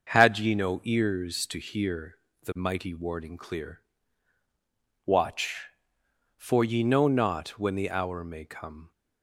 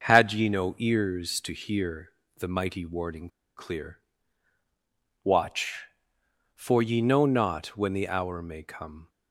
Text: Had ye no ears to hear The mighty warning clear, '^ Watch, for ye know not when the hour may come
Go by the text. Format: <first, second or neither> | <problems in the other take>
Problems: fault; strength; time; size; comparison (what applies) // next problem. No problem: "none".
first | starts louder than the rest; until 1.1 s; 7 dB; also in the first // pauses between "hear" and "The"; slight; at 2.0 s; 0.26 s long; slight in the first // pauses between "warning" and "clear"; slight; at 3.2 s; 0.28 s long